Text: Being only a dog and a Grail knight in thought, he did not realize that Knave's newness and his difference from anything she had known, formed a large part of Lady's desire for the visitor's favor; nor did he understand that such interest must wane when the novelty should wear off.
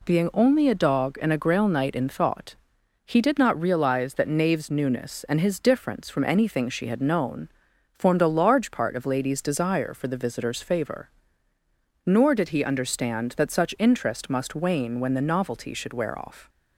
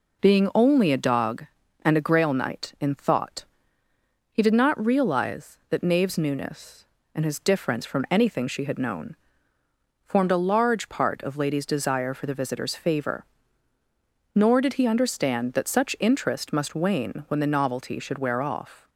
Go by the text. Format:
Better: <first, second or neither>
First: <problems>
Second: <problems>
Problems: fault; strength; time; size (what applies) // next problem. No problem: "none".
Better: neither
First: none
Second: none